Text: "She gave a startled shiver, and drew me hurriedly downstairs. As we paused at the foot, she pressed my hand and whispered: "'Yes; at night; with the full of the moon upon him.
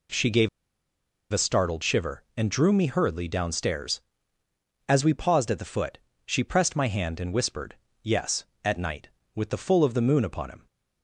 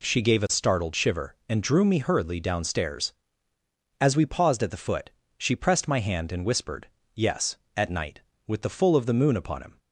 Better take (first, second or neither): second